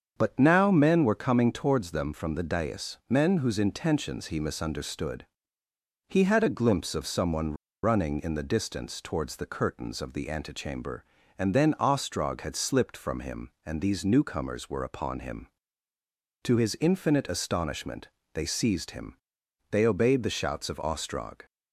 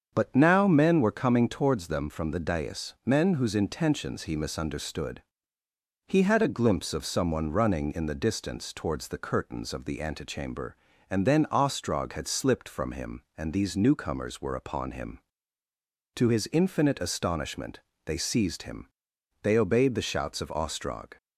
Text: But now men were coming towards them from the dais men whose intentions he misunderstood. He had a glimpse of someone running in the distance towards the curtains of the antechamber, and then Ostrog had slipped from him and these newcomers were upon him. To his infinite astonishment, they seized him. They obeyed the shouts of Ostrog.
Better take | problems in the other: second | starts louder than the rest; strong; until 1.2 s; 7 dB; strong in the second // pauses between "someone" and "running"; slight; at 7.5 s; 0.29 s long

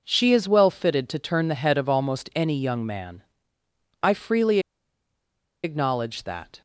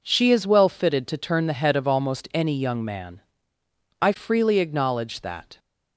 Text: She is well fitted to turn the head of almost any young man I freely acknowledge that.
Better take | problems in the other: second | pauses between "man" and "I"; noticeable; at 3.2 s; 0.78 s long; noticeable in the second // pauses between "freely" and "acknowledge"; at 4.5 s; 1.0 s long

